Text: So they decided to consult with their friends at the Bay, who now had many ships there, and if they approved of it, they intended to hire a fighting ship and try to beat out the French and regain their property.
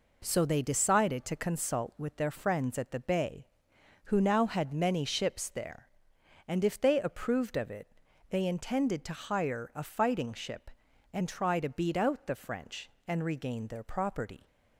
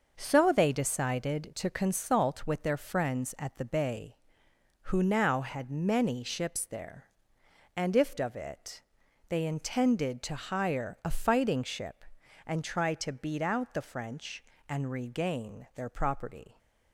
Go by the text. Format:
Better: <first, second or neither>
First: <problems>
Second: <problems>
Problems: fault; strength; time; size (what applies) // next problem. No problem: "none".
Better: first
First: none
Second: starts louder than the rest; until 1.1 s; 6 dB // skips "they approved"; at 8.1 s